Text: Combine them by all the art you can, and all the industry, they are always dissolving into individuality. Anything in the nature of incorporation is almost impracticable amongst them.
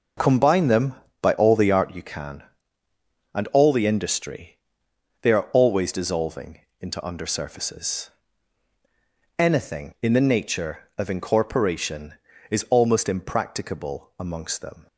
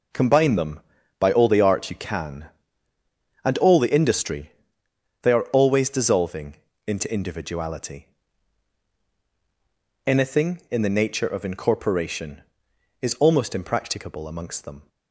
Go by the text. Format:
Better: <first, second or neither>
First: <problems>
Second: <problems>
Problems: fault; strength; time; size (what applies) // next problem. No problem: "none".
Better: second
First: pauses between "dissolving" and "into"; slight; at 6.6 s; 0.20 s long // says "undersurfaces" for "individuality"; at 7.0 s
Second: pauses between "dissolving" and "into"; slight; at 6.5 s; 0.30 s long